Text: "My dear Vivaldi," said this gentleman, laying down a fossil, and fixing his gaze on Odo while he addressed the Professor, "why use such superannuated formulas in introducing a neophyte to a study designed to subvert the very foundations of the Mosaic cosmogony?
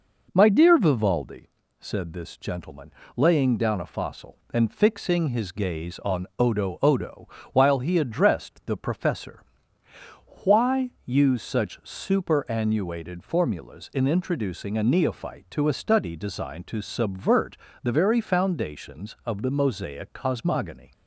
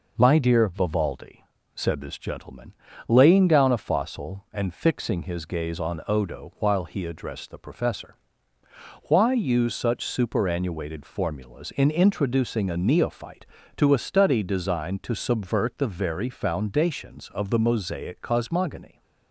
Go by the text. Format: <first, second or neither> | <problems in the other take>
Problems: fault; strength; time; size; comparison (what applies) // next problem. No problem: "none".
second | says "Odo" twice; at 6.8 s // pauses between "subvert" and "the"; slight; at 17.5 s; 0.24 s long